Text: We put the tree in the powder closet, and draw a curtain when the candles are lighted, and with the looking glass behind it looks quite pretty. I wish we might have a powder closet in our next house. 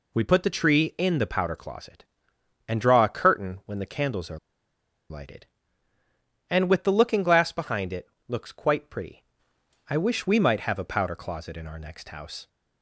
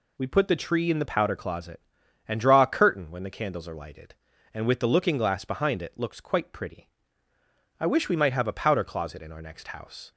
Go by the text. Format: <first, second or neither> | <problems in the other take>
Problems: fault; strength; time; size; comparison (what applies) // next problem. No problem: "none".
second | pauses between "are" and "lighted"; noticeable; at 4.3 s; 0.71 s long // pauses between "it" and "looks"; slight; at 8.0 s; 0.22 s long